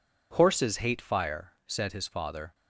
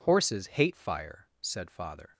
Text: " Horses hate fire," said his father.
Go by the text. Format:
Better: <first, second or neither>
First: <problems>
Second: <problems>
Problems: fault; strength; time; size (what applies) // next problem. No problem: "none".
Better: first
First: none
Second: skips "his"; at 1.6 s